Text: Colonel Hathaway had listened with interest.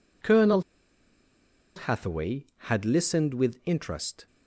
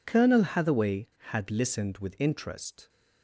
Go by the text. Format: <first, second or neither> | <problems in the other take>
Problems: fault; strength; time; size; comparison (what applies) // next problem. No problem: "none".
second | pauses between "Colonel" and "Hathaway"; at 0.6 s; 1.1 s long